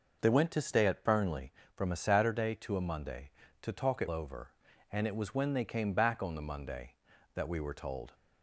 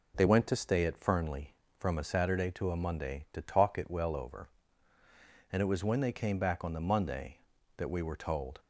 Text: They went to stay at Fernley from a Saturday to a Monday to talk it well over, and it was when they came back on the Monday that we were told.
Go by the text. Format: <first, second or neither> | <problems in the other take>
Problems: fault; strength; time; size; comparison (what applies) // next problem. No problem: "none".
second | skips "well"; at 4.0 s